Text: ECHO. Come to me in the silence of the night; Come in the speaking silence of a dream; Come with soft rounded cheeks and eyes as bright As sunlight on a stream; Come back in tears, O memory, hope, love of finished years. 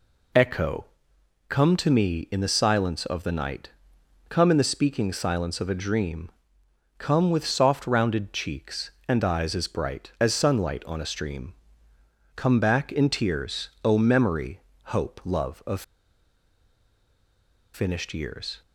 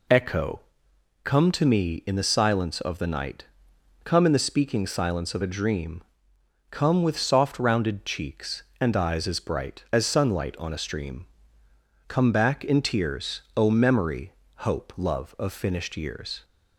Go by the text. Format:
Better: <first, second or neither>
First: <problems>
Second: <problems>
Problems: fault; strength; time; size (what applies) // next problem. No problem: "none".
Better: second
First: pauses between "of" and "finished"; strong; at 15.8 s; 1.9 s long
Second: none